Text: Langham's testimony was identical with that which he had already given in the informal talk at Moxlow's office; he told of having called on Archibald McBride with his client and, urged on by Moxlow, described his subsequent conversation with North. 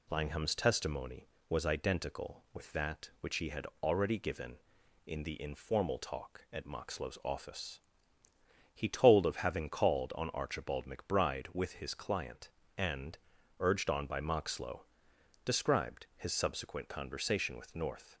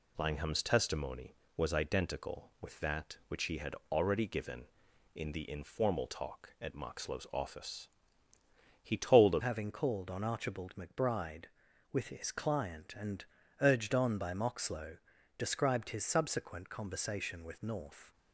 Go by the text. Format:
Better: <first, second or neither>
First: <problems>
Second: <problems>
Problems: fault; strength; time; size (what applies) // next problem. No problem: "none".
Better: first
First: pauses between "had" and "already"; slight; at 3.6 s; 0.16 s long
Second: pauses between "had" and "already"; slight; at 3.7 s; 0.16 s long // changes voice at "having"; from 9.4 s on; 8.7 s long